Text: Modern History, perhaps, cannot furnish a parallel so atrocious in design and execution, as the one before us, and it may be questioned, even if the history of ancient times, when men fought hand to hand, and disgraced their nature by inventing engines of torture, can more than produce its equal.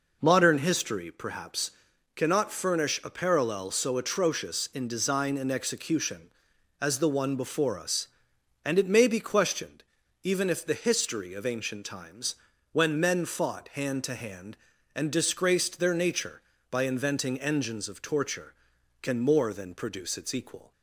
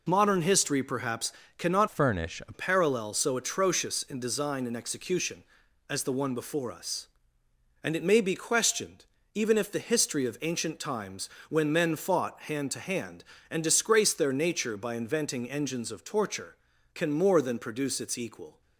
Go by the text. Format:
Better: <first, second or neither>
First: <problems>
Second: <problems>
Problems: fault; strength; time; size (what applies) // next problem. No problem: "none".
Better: first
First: none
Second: changes voice from "furnish" to "a"; from 1.8 to 2.5 s; 0.7 s long